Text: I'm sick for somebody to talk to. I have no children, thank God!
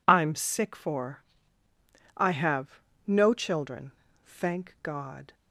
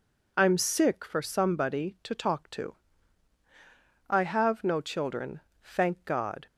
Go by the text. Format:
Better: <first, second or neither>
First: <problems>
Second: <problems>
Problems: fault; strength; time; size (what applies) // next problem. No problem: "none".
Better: second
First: skips "somebody to talk to"; at 1.6 s // pauses between "have" and "no"; slight; at 2.7 s; 0.28 s long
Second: none